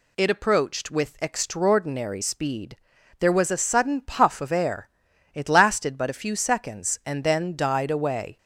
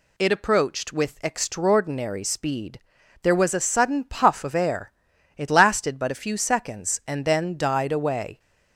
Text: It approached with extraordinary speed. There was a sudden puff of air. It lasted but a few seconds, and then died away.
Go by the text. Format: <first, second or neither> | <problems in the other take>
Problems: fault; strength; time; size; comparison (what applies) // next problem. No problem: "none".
neither | none